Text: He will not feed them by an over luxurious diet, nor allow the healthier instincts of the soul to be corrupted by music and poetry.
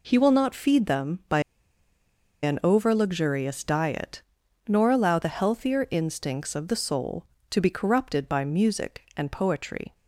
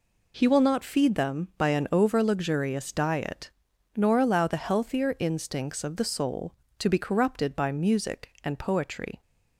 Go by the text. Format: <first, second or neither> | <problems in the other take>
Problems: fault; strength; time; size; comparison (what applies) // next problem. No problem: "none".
second | pauses between "by" and "an"; at 1.3 s; 1.0 s long